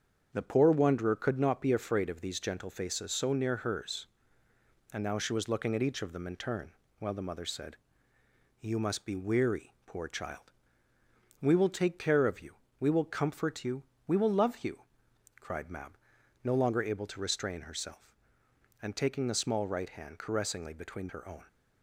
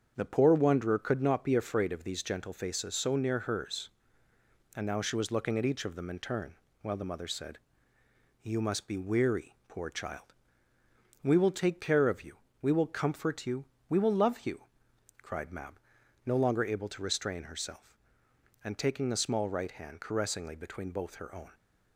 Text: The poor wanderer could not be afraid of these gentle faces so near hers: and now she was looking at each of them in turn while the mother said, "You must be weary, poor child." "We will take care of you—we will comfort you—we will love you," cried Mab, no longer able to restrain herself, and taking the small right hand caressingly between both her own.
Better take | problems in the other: second | starts louder than the rest; strong; until 1.3 s; 7.5 dB; strong in the second // pauses between "turn" and "while"; slight; at 6.7 s; 0.26 s long; slight in the second // skips "both"; at 21.0 s

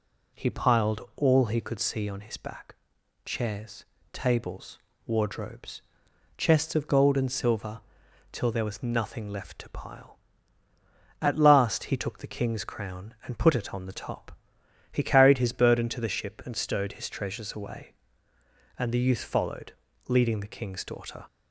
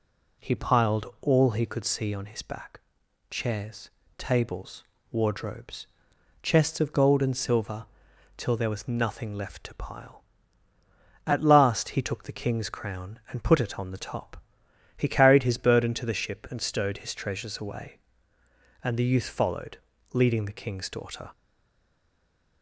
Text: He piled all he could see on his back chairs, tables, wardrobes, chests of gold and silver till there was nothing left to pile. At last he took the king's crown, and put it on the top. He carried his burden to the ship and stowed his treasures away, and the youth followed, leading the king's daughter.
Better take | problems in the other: first | pauses between "back" and "chairs"; noticeable; at 2.7 s; 0.50 s long; noticeable in the first // pauses between "silver" and "till"; noticeable; at 7.8 s; 0.52 s long; noticeable in the first // stays silent after the last word; noticeable; from 21.3 s on; 1.3 s long

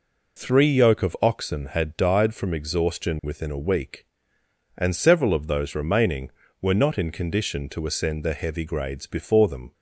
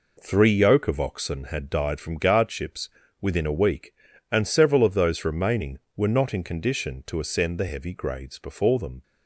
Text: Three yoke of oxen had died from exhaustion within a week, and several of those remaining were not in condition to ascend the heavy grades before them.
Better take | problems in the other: first | says "guardships" for "exhaustion"; at 2.1 s

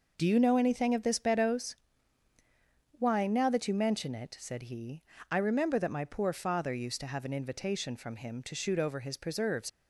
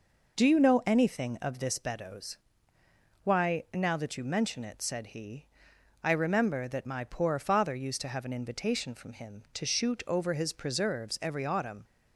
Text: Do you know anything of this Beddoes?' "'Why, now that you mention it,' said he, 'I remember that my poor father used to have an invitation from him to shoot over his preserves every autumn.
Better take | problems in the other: second | stops before "every autumn"; at 9.6 s

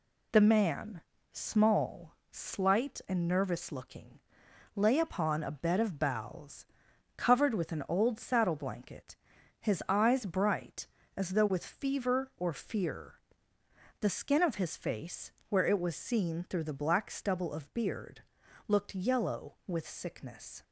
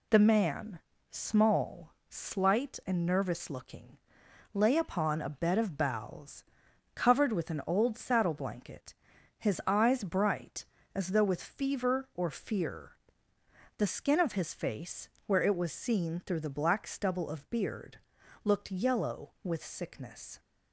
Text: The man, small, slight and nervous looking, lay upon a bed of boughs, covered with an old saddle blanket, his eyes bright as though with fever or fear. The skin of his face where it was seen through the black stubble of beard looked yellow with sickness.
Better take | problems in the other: neither | pauses between "face" and "where"; slight; the same in both // pauses between "beard" and "looked"; noticeable; the same in both

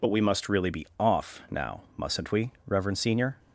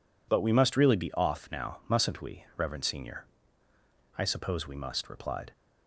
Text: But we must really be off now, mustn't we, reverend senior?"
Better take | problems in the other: first | goes on to say "I suppose we must replied"; from 4.1 s on; 1.3 s long

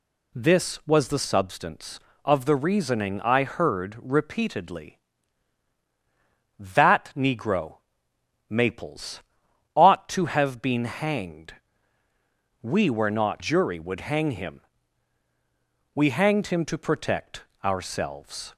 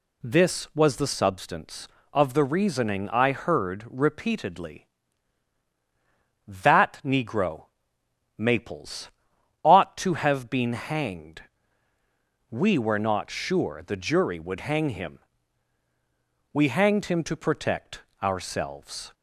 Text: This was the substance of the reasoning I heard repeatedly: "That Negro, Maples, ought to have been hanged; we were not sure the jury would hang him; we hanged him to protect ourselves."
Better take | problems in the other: second | skips "sure the"; at 13.4 s // pauses between "protect" and "ourselves"; slight; at 17.4 s; 0.20 s long; slight in the second

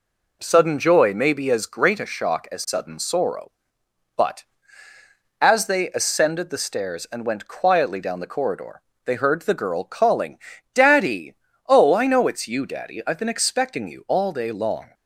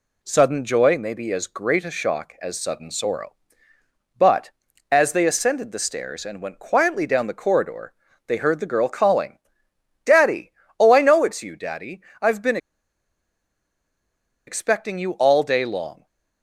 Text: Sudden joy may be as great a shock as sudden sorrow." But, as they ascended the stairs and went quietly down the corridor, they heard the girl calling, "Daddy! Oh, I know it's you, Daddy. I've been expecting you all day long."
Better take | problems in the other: first | pauses between "been" and "expecting"; strong; at 12.5 s; 1.8 s long

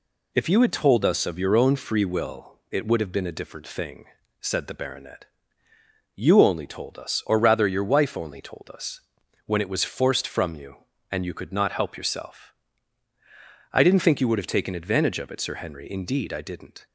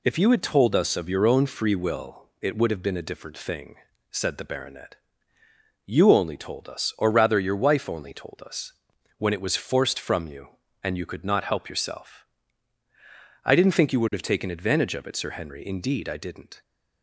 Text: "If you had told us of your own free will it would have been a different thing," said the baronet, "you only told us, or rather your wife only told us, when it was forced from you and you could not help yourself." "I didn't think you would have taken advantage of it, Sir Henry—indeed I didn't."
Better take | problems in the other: neither | none

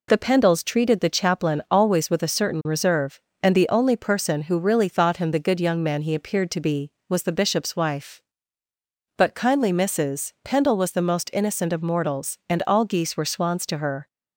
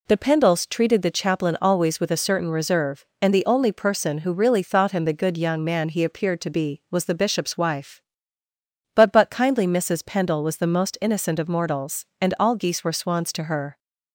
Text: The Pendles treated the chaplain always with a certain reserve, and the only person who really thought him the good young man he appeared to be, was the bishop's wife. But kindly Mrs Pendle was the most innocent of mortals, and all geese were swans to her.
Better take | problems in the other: first | says "But" twice; at 9.1 s

